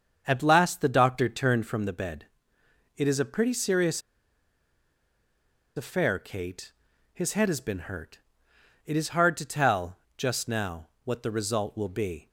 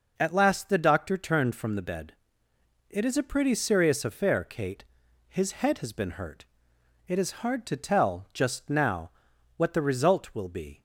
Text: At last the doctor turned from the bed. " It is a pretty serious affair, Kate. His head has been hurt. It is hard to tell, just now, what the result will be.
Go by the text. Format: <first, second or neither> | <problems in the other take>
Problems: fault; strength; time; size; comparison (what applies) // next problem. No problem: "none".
second | starts louder than the rest; until 1.2 s; 7 dB // pauses between "serious" and "affair"; strong; at 4.0 s; 1.7 s long